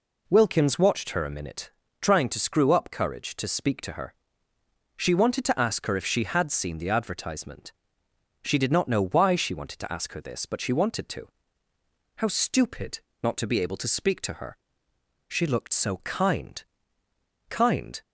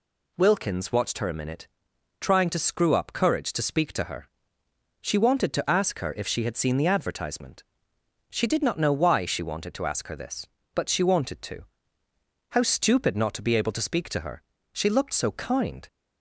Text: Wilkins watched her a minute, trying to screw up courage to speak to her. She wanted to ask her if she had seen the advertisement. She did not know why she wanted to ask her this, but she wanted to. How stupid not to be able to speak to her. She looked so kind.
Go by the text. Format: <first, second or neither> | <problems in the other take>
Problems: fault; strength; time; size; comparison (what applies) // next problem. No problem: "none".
second | pauses between "stupid" and "not"; slight; at 12.9 s; 0.22 s long // says "kind" twice; at 17.4 s